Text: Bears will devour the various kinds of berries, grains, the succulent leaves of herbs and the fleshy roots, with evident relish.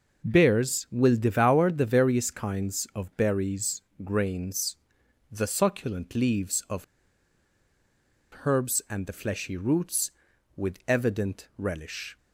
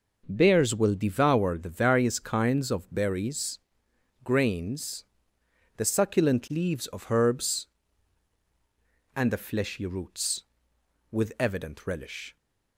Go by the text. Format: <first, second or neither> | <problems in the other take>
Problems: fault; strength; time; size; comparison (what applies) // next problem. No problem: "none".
second | pauses between "of" and "herbs"; strong; at 6.8 s; 1.6 s long